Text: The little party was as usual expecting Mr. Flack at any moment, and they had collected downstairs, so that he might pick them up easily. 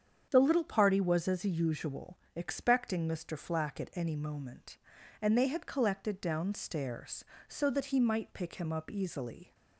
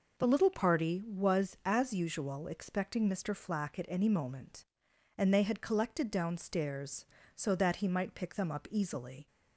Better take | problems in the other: second | starts louder than the rest; strong; until 1.3 s; 8 dB // pauses between "usual" and "expecting"; slight; at 2.1 s; 0.16 s long // says "him" for "them"; at 8.5 s

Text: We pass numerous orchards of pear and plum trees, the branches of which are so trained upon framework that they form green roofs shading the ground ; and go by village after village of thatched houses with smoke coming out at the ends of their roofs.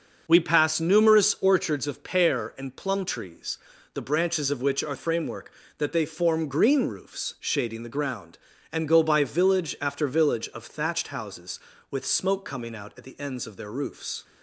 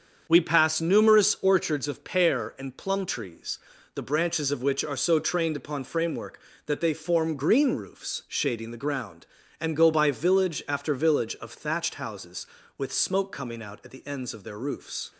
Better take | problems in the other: second | starts louder than the rest; until 1.2 s; 6 dB; also in the second // skips "so trained upon"; at 4.9 s

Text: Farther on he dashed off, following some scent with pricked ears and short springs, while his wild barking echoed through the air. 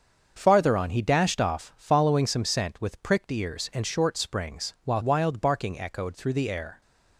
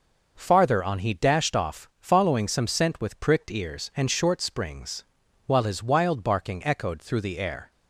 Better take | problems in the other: second | starts louder than the rest; until 1.3 s; 7 dB // skips "his"; at 5.0 s

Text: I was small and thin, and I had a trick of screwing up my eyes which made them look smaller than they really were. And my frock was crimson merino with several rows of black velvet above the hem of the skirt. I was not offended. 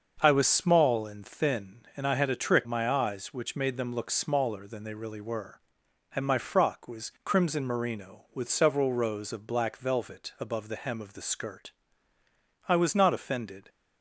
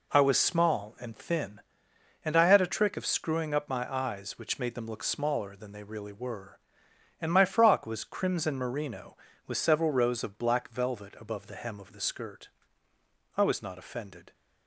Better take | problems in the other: second | starts louder than the rest; until 1.2 s; 6 dB // skips "of screwing up"; at 2.6 s

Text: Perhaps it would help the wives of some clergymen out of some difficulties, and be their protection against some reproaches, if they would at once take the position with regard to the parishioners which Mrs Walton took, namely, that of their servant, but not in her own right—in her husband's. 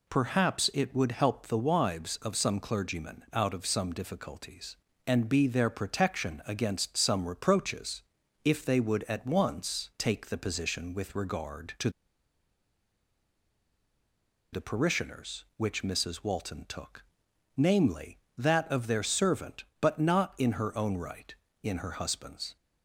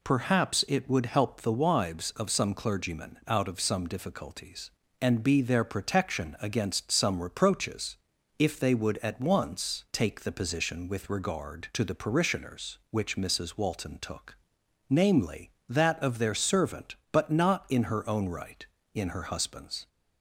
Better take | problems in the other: second | pauses between "to" and "the"; strong; at 11.8 s; 2.6 s long

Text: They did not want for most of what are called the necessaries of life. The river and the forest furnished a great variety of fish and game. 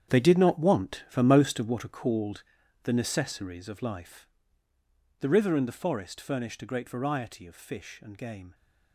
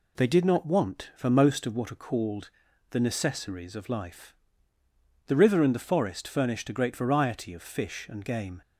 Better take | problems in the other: second | gets quieter; strong; throughout; 12.5 dB // pauses between "called" and "the"; at 2.4 s; 0.42 s long; also in the second

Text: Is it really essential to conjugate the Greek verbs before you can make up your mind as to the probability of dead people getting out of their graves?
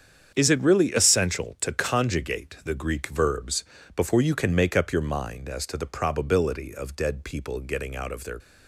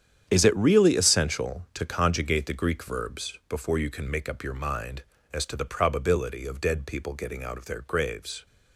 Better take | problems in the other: second | starts louder than the rest; strong; until 1.3 s; 7.5 dB; strong in the second // pauses between "verbs" and "before"; slight; at 3.6 s; 0.30 s long // stops before "graves"; at 8.3 s

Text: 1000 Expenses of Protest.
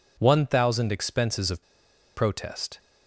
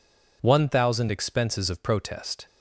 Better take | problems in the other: second | pauses between "of" and "Protest"; noticeable; at 1.6 s; 0.53 s long

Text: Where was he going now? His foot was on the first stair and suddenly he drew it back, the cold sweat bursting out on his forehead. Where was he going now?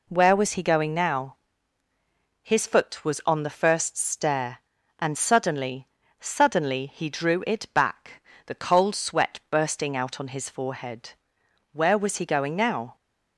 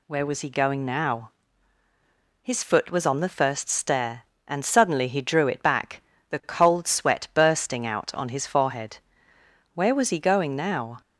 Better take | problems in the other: second | says "suddenly" twice; at 6.1 s

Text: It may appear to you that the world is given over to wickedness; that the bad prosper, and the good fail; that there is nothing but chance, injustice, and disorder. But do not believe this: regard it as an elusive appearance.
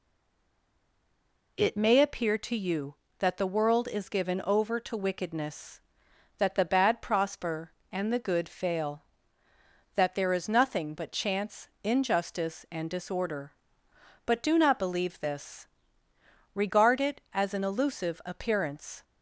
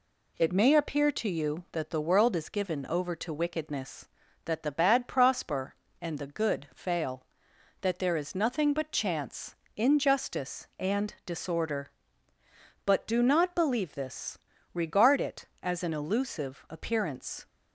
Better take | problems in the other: second | stays silent before the first word; noticeable; until 1.5 s; 1.5 s long

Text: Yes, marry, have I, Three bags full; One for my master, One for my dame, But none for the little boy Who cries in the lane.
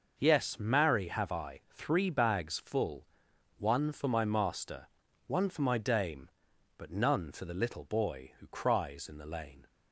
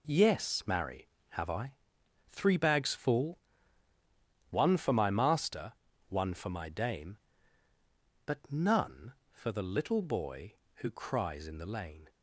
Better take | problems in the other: neither | none

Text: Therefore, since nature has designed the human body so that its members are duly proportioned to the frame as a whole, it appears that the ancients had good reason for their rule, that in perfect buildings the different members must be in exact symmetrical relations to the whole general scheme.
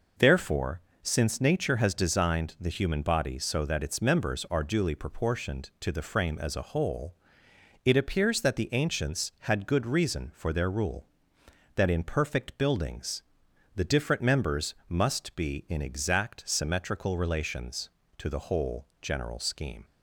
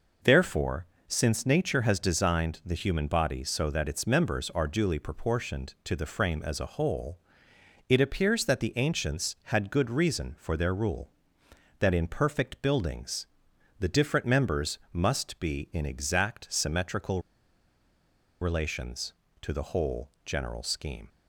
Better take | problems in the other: first | pauses between "buildings" and "the"; noticeable; at 13.2 s; 0.52 s long; noticeable in the first // pauses between "symmetrical" and "relations"; at 17.2 s; 1.2 s long

